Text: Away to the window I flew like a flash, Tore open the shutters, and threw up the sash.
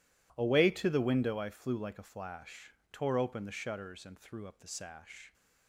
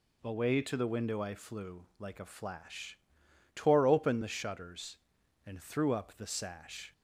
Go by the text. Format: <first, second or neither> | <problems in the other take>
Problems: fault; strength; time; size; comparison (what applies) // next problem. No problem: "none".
neither | none